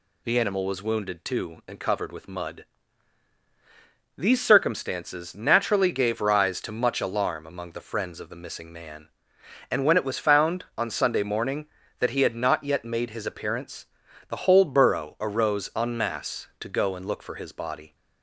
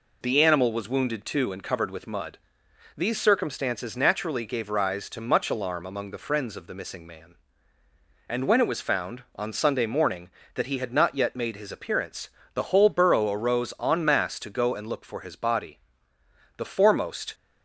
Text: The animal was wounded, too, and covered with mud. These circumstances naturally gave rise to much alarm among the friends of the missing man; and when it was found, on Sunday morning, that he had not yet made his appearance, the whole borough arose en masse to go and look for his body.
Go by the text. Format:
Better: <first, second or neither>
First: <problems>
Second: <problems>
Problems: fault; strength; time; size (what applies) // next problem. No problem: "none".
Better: first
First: none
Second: goes on to say "The foremost"; noticeable; from 16.5 s on; 0.76 s long